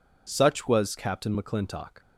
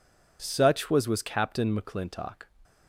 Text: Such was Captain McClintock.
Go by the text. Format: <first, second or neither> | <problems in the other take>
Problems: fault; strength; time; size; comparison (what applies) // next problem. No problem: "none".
first | says "was" twice; at 1.0 s